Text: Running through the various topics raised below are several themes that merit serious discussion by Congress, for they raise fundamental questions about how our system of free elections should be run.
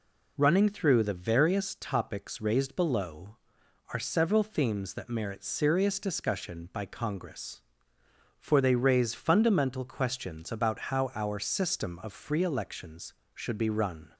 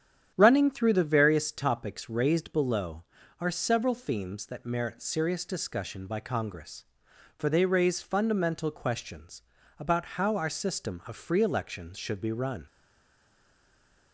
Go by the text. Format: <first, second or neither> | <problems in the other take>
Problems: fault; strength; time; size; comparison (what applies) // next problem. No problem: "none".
first | starts louder than the rest; strong; until 1.3 s; 9 dB // pauses between "questions" and "about"; slight; at 9.4 s; 0.36 s long // stays silent after the last word; noticeable; from 12.6 s on; 1.5 s long